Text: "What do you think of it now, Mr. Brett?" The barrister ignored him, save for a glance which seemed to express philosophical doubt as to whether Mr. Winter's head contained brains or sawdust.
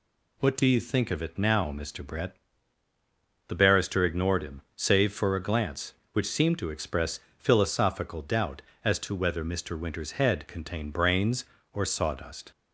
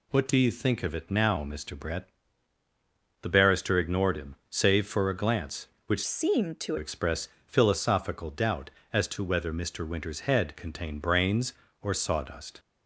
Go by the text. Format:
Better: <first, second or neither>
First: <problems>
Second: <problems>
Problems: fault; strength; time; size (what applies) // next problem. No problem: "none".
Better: first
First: pauses between "express" and "philosophical"; slight; at 7.2 s; 0.18 s long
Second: changes voice from "seemed" to "to"; from 6.0 to 6.7 s; 0.7 s long // pauses between "express" and "philosophical"; slight; at 7.2 s; 0.18 s long